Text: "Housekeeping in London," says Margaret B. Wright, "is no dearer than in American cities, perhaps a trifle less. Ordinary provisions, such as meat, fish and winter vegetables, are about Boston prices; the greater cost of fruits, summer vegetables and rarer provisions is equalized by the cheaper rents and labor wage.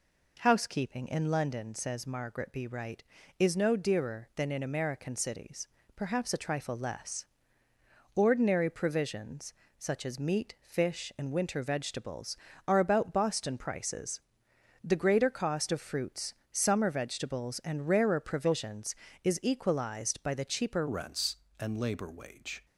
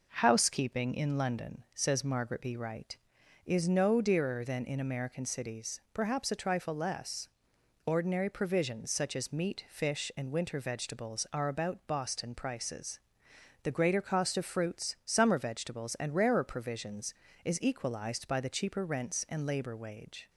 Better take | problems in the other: second | changes voice at "rents"; from 20.8 s on; 1.8 s long

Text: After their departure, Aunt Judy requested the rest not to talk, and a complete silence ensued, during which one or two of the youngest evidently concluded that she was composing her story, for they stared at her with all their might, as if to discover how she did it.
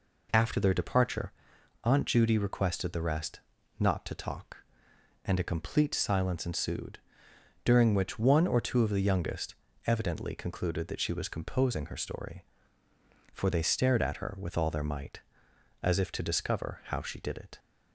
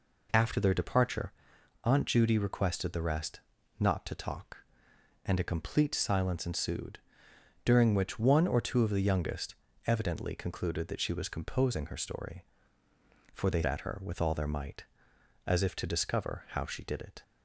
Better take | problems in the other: first | pauses between "rest" and "not"; at 3.4 s; 0.40 s long; also in the first // pauses between "youngest" and "evidently"; slight; at 9.5 s; 0.32 s long; slight in the first // skips "stared"; at 13.6 s

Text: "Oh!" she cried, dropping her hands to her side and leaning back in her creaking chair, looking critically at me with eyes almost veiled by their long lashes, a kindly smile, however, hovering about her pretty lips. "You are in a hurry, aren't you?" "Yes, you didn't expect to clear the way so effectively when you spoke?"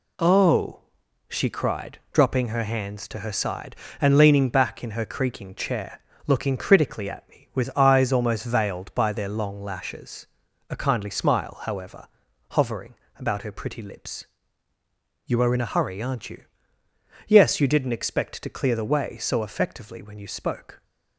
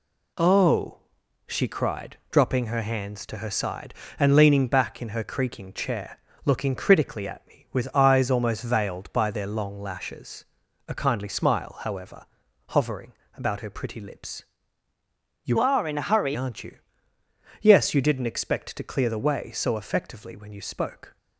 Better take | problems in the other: first | pauses between "hovering" and "about"; slight; at 13.1 s; 0.24 s long; slight in the first // changes voice from "are" to "hurry"; from 15.5 to 16.3 s; 0.8 s long

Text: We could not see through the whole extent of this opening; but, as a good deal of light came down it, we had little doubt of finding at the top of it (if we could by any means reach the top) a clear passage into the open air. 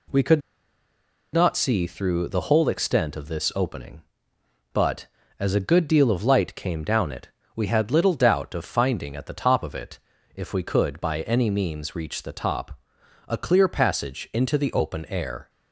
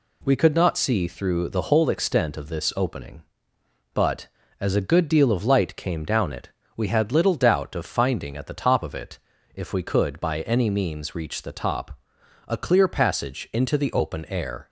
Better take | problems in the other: second | pauses between "could" and "not"; noticeable; at 0.4 s; 0.92 s long

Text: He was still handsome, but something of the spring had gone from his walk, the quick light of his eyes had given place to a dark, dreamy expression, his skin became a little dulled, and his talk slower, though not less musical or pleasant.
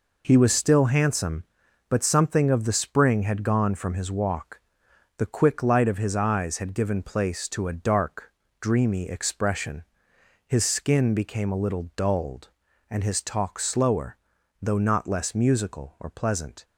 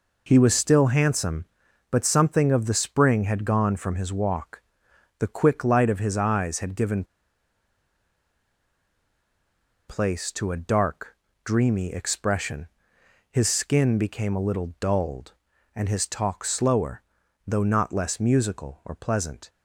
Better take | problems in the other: first | pauses between "given" and "place"; strong; at 7.0 s; 2.8 s long

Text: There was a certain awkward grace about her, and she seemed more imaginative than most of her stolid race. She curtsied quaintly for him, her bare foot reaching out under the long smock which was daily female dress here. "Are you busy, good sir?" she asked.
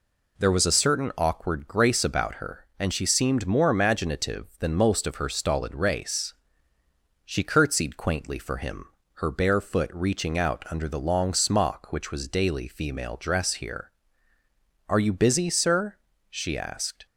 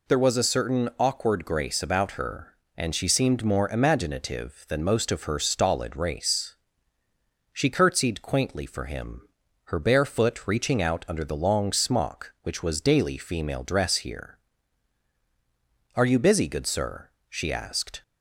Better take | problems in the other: second | skips "good"; at 15.4 s

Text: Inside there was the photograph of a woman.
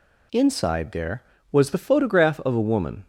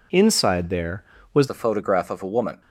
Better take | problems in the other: first | changes voice at "the"; from 1.4 s on; 1.2 s long

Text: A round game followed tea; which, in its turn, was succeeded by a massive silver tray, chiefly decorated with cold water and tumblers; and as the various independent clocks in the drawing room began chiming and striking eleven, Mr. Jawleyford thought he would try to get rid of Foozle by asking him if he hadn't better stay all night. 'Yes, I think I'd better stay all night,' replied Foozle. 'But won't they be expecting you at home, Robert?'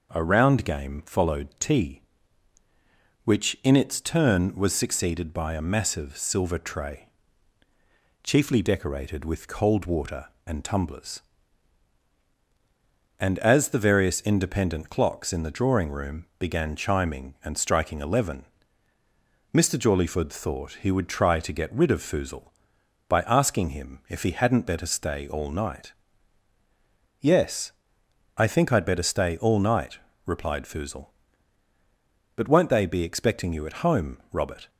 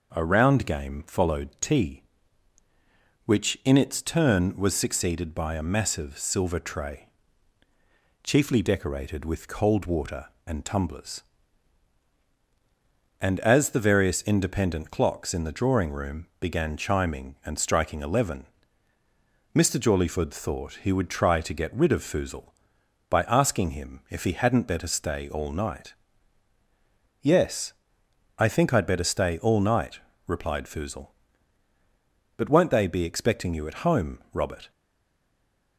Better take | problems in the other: first | stays silent after the last word; from 34.7 s on; 1.0 s long

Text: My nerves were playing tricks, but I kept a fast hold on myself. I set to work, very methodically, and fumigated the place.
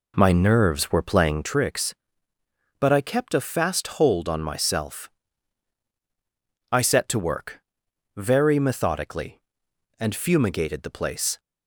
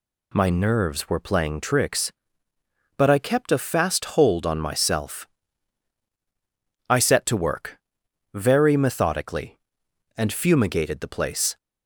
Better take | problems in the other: second | starts louder than the rest; slight; until 1.6 s; 3 dB

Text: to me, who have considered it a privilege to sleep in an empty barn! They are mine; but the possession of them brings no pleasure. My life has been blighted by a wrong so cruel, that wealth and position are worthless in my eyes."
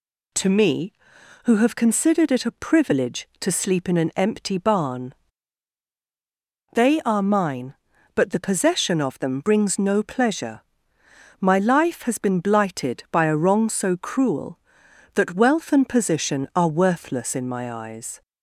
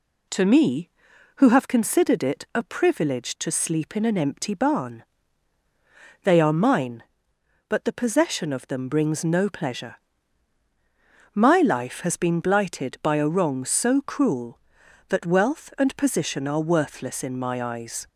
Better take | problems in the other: neither | none

